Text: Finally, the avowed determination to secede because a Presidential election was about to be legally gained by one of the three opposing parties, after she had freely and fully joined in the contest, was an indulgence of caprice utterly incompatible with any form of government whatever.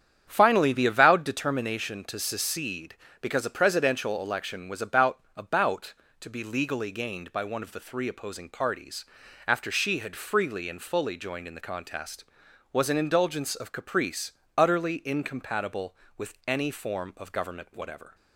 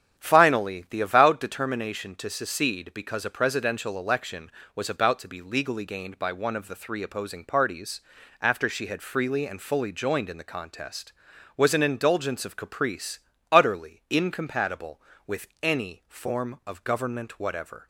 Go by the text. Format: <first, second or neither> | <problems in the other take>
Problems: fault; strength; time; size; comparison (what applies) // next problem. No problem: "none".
second | starts louder than the rest; strong; until 1.2 s; 8.5 dB; strong in the second // says "about" twice; at 5.3 s // pauses between "caprice" and "utterly"; slight; at 14.3 s; 0.24 s long; slight in the second